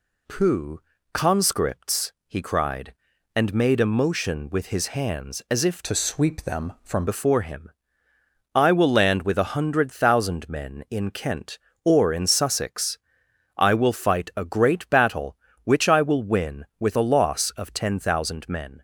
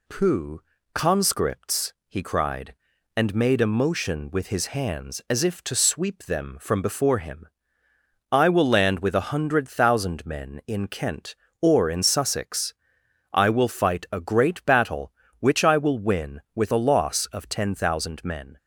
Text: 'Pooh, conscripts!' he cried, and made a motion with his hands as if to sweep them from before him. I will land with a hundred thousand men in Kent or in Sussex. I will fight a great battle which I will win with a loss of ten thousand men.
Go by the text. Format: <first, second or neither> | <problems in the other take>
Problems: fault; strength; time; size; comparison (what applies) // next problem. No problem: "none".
second | changes voice from "to" to "from"; from 5.8 to 7.0 s; 1.2 s long